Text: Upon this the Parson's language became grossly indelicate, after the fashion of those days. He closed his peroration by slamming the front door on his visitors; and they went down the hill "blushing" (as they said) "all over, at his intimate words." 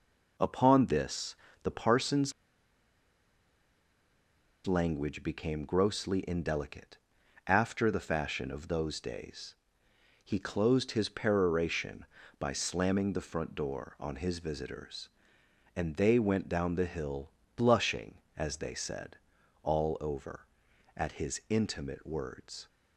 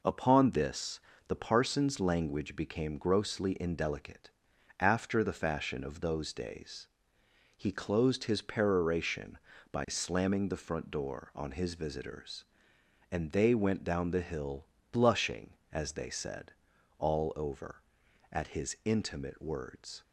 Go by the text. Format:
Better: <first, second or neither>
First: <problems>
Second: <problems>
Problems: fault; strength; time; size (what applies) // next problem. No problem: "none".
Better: second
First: pauses between "this" and "the"; slight; at 1.3 s; 0.28 s long // pauses between "Parson's" and "language"; strong; at 2.3 s; 2.3 s long // pauses between "hill" and "blushing"; slight; at 17.3 s; 0.24 s long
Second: pauses between "this" and "the"; slight; at 0.9 s; 0.28 s long // pauses between "hill" and "blushing"; slight; at 14.6 s; 0.24 s long